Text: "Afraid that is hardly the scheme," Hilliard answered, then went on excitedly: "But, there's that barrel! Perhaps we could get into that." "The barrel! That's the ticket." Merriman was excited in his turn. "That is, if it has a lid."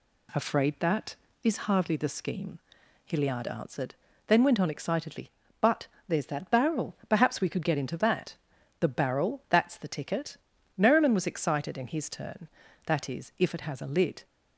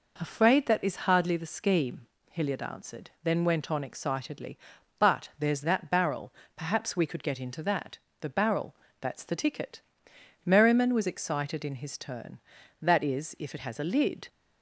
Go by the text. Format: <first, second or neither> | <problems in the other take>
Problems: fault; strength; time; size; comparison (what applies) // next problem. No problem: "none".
neither | none